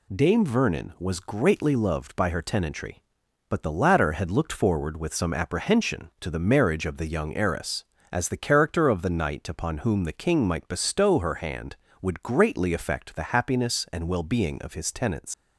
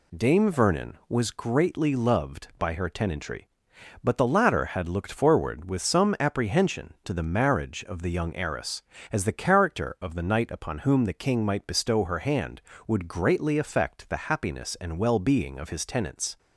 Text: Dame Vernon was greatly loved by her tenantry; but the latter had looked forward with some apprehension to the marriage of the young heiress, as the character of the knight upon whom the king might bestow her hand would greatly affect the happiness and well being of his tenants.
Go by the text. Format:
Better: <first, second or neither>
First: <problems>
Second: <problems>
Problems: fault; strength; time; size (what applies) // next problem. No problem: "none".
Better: second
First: leaves "tenants" unfinished; at 15.3 s; 90 ms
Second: none